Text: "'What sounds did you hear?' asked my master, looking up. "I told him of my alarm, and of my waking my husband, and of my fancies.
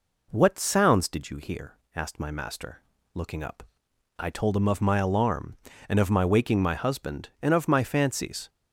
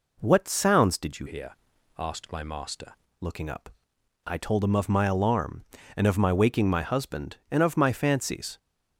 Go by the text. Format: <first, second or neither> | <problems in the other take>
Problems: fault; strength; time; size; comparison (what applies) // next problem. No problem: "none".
first | changes voice from "hear" to "master"; from 1.2 to 2.9 s; 1.7 s long